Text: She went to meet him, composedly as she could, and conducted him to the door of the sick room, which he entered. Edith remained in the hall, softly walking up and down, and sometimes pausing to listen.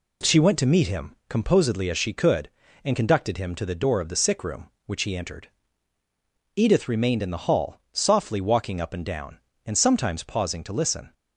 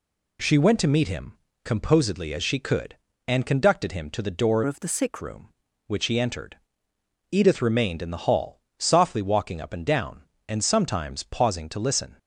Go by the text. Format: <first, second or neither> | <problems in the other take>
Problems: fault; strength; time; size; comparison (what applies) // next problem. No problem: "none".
first | changes voice from "of" to "sick"; from 4.6 to 5.2 s; 0.6 s long